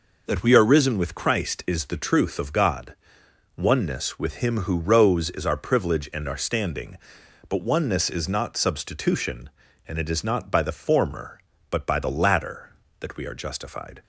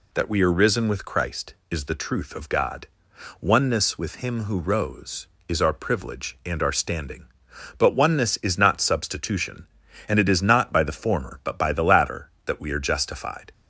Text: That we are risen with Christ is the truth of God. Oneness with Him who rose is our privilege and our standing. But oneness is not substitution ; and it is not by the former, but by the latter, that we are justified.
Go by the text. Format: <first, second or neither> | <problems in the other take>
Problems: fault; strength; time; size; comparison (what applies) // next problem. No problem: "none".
neither | none